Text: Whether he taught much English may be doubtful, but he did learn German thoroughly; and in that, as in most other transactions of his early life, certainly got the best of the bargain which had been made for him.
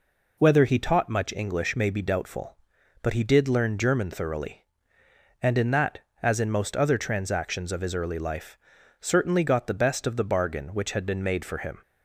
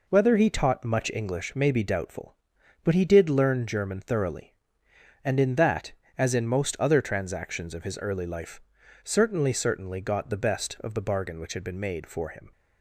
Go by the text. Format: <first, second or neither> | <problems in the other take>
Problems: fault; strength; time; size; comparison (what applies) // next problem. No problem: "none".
first | says "certainly" twice; at 9.5 s